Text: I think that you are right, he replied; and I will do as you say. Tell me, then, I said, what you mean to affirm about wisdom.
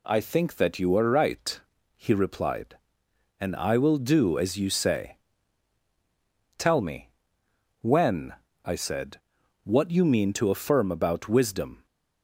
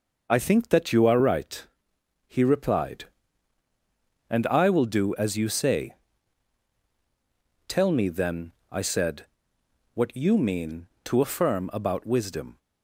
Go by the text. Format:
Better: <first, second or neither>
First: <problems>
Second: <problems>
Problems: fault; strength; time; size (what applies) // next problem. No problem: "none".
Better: second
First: says "when" for "then"; at 7.8 s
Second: none